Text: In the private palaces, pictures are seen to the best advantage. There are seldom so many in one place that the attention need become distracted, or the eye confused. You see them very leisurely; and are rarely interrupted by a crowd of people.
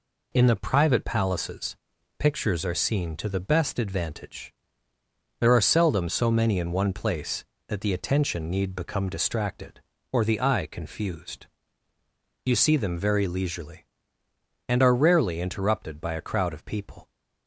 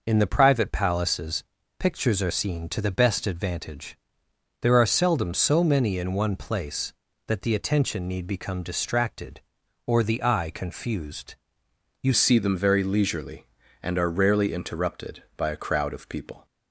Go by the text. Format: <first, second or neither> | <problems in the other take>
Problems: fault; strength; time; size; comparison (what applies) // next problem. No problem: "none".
first | changes voice at "see"; from 12.1 s on; 4.3 s long